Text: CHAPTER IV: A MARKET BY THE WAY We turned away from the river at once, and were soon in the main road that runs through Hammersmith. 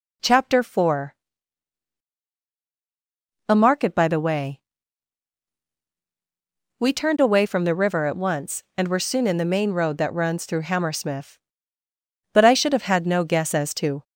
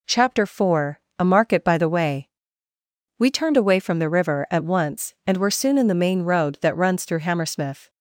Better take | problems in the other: second | pauses between "WAY" and "We"; strong; at 4.5 s; 2.1 s long; noticeable in the second // goes on to say "But I should have had no guess as to"; strong; from 12.3 s on; 1.7 s long

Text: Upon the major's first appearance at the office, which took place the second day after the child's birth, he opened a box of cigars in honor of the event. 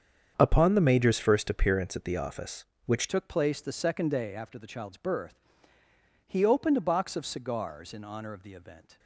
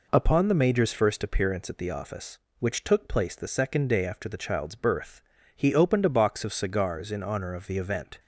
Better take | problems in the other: second | starts louder than the rest; strong; until 1.3 s; 7.5 dB // changes voice at "took"; from 3.0 s on; 5.9 s long

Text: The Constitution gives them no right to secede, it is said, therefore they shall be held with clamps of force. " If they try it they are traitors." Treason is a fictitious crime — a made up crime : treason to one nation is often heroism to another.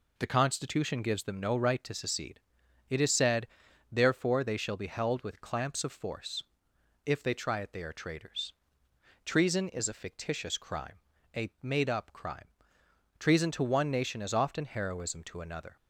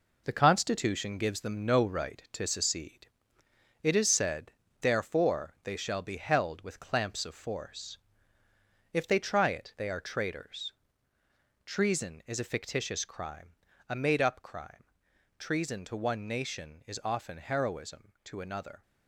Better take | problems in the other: first | gets quieter; strong; throughout; 7.5 dB

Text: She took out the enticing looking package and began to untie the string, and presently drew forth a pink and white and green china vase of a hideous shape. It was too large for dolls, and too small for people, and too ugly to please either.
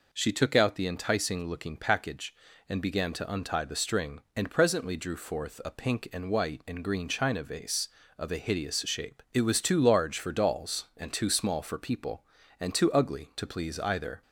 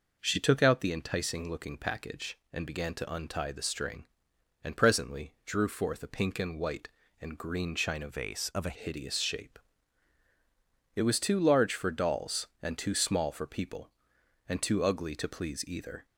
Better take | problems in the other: first | changes voice from "vase" to "a"; from 8.0 to 8.7 s; 0.7 s long

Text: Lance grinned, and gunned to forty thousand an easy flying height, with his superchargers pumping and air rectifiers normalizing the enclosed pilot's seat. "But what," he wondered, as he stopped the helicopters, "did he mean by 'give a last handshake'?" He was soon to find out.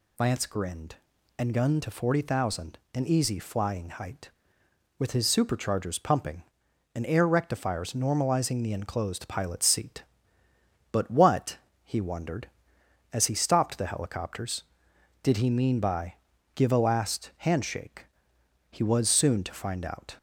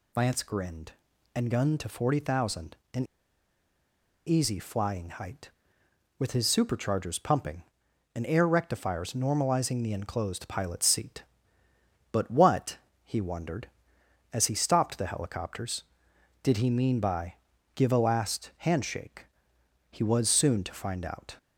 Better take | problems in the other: first | pauses between "thousand" and "an"; slight; at 2.7 s; 0.18 s long; slight in the first // pauses between "an" and "easy"; at 3.0 s; 1.2 s long // pauses between "by" and "give"; at 17.3 s; 0.40 s long; also in the first

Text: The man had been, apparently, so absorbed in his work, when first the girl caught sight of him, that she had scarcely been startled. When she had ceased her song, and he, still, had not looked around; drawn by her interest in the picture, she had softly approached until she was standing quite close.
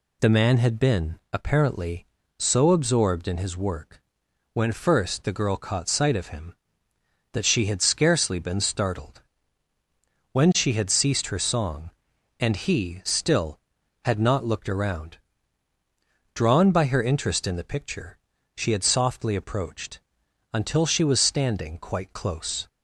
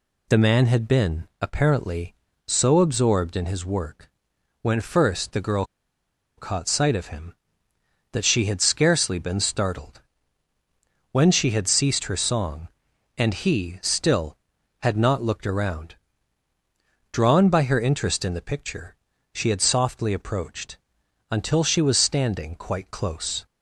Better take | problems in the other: first | pauses between "girl" and "caught"; noticeable; at 5.6 s; 0.73 s long // pauses between "approached" and "until"; noticeable; at 20.7 s; 0.54 s long; noticeable in the first

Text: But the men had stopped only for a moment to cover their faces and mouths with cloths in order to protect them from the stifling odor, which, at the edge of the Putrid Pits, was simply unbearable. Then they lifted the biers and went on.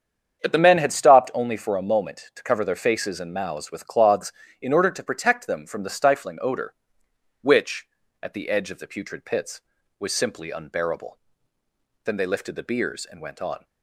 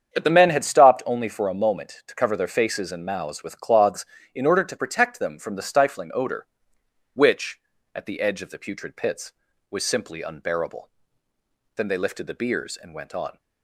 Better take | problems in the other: neither | starts louder than the rest; strong; the same in both

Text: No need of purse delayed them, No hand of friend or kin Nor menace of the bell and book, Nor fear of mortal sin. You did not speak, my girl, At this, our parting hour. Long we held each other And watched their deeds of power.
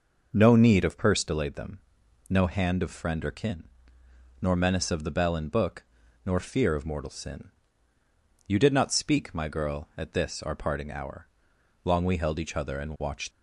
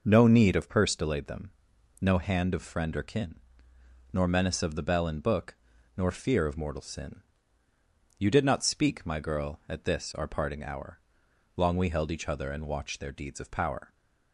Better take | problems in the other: second | pauses between "kin" and "Nor"; noticeable; at 3.6 s; 0.76 s long; noticeable in the second // stops before "their deeds of power"; at 13.3 s

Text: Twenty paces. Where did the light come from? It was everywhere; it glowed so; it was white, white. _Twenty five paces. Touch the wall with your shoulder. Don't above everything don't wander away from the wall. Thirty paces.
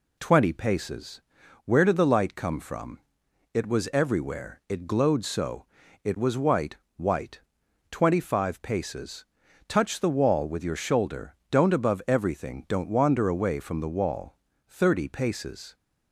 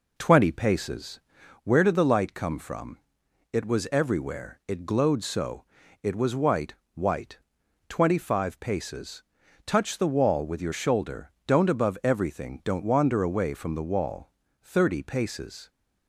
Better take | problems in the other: first | starts louder than the rest; noticeable; until 1.8 s; 4 dB

